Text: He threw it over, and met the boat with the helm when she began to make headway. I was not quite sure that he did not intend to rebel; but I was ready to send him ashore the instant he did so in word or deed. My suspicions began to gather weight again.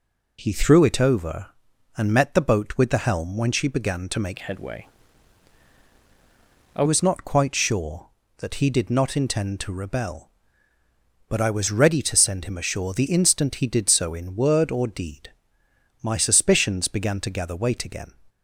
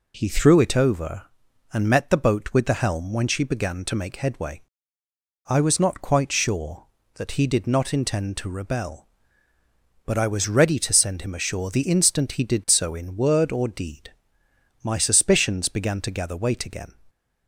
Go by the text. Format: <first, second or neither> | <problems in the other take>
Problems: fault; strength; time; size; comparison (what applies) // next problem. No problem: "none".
second | changes voice from "headway" to "I"; from 4.4 to 6.8 s; 2.4 s long